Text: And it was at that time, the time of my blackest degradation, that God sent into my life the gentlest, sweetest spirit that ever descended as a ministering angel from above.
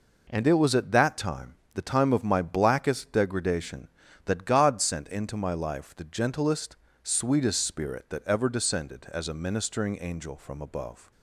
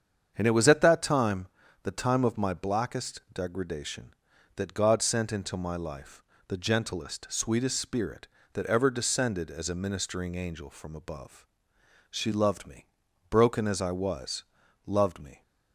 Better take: first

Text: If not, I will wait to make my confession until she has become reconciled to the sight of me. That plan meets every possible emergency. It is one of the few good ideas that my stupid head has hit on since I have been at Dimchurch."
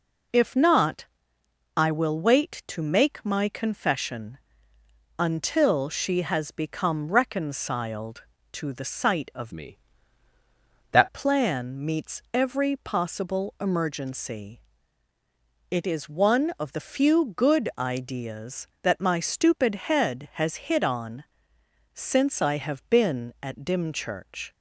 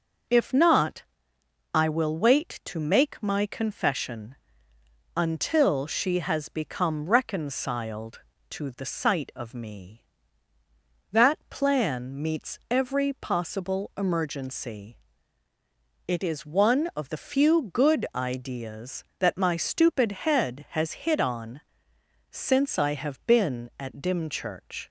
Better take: second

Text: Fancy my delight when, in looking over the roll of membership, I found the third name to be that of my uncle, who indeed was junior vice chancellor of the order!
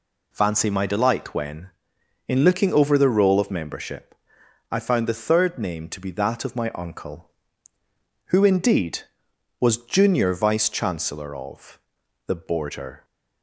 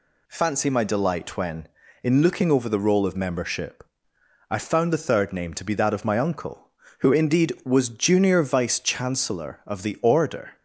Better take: second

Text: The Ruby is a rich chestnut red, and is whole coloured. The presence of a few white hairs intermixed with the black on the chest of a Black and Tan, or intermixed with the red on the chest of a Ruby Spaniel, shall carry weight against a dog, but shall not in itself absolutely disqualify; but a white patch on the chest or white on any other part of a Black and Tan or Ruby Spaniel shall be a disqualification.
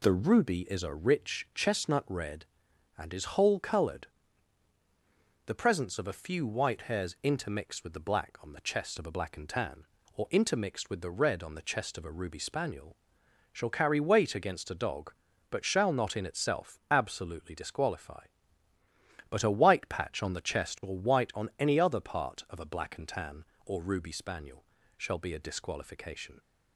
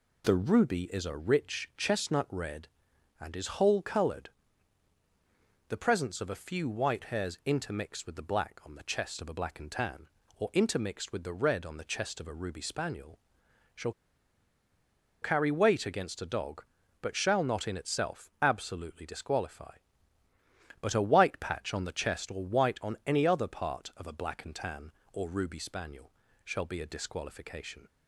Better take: first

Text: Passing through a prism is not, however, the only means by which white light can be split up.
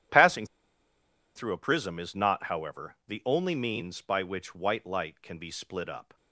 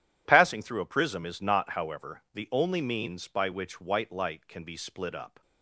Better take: second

